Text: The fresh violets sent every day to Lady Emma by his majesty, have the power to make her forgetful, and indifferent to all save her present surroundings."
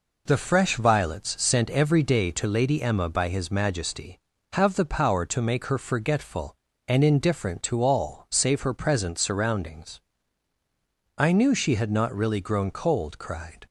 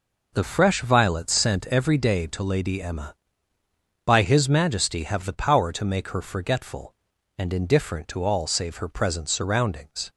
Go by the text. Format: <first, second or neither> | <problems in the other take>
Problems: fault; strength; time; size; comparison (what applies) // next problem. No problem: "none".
second | goes on to say "I knew she had not really grown cold cried"; strong; from 11.1 s on; 2.4 s long